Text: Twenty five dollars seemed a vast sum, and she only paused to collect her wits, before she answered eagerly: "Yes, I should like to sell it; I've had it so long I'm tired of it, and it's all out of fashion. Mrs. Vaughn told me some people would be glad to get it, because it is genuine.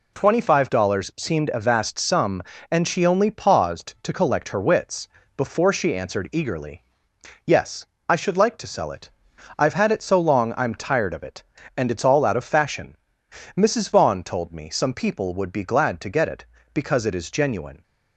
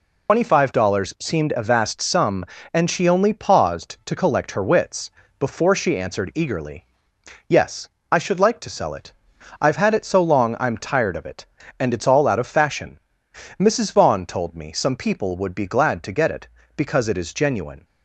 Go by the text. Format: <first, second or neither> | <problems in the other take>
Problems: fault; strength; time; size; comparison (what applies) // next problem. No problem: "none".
first | loses the start of "Twenty"; at 0.2 s; 130 ms